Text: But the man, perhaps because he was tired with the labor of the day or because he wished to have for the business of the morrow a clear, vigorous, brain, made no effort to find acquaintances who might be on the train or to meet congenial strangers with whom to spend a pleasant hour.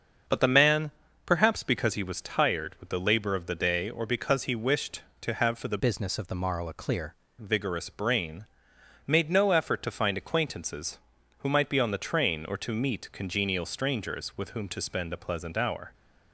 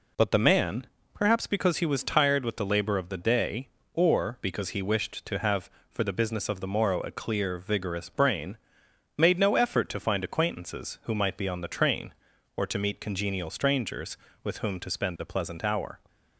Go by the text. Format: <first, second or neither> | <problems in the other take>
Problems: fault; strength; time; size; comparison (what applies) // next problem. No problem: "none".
second | starts louder than the rest; until 1.6 s; 6.5 dB // changes voice from "business" to "clear"; from 5.7 to 7.1 s; 1.4 s long